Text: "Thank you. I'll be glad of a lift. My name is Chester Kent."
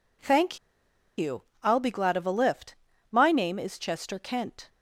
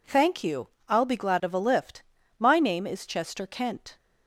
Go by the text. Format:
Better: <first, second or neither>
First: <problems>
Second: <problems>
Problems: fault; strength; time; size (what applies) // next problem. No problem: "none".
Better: second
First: pauses between "Thank" and "you"; noticeable; at 0.5 s; 0.60 s long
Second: none